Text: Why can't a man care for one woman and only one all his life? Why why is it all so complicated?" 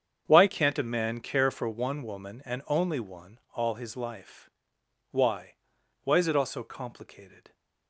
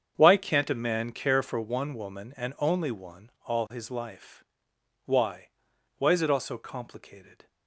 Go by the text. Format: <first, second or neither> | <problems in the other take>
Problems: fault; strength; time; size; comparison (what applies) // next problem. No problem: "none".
neither | starts louder than the rest; strong; the same in both // pauses between "Why" and "why"; noticeable; the same in both